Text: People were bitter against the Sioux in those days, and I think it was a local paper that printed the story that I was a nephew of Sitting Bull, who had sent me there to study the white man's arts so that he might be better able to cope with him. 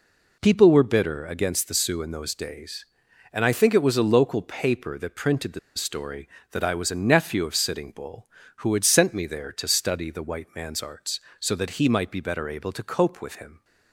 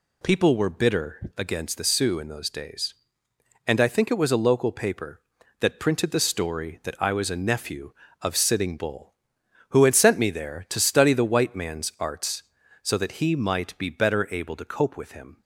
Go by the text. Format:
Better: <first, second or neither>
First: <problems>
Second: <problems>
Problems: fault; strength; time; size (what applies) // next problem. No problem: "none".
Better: second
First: pauses between "the" and "story"; slight; at 5.5 s; 0.16 s long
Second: none